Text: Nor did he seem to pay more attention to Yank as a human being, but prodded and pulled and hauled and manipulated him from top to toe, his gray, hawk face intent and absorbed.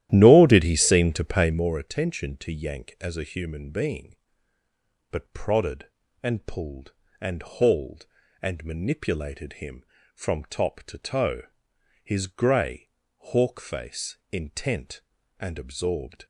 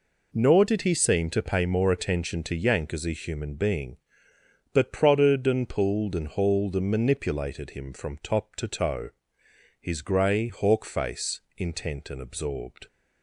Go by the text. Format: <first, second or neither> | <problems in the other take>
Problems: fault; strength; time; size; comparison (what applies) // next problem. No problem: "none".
second | starts louder than the rest; strong; until 1.7 s; 13 dB // pauses between "face" and "intent"; slight; at 14.1 s; 0.15 s long; slight in the second